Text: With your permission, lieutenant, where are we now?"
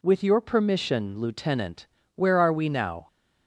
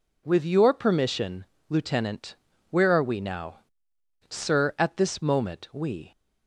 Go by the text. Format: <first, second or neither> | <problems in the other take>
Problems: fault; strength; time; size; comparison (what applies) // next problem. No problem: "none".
first | goes on to say "Sir at this moment we"; strong; from 4.2 s on; 1.8 s long